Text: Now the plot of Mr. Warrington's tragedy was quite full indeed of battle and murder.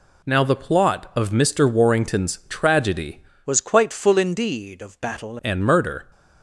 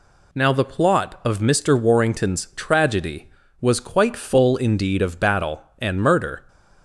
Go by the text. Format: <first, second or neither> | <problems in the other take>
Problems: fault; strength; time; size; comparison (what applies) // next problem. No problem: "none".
second | changes voice from "was" to "battle"; from 3.4 to 5.3 s; 1.9 s long